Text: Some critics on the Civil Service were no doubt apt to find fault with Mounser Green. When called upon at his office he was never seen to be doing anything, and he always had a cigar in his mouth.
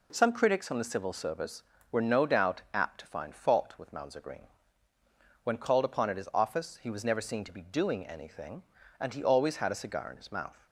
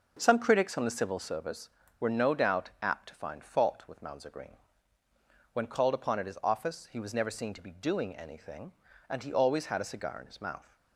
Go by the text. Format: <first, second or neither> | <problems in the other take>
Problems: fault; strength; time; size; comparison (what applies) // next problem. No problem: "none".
first | starts louder than the rest; noticeable; until 1.3 s; 6 dB